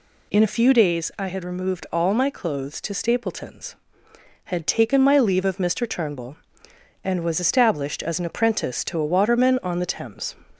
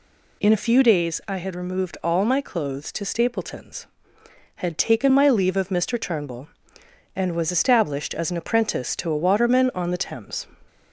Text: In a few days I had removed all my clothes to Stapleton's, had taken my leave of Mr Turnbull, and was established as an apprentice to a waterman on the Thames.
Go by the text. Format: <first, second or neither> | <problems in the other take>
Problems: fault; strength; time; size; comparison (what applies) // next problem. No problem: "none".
neither | none